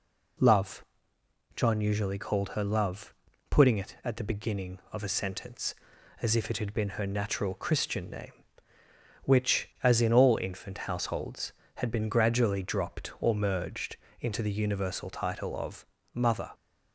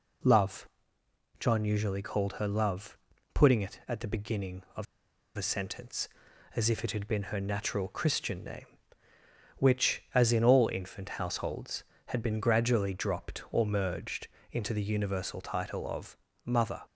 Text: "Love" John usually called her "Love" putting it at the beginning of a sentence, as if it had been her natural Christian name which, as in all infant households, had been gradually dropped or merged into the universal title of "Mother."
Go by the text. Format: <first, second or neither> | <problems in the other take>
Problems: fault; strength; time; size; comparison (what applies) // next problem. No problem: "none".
first | pauses between "Love" and "John"; noticeable; at 0.6 s; 0.72 s long; noticeable in the first // pauses between "Love" and "putting"; at 2.9 s; 0.38 s long; also in the first // pauses between "of" and "a"; noticeable; at 4.8 s; 0.50 s long // pauses between "merged" and "into"; slight; at 14.2 s; 0.22 s long; slight in the first // pauses between "of" and "Mother"; slight; at 16.1 s; 0.30 s long; slight in the first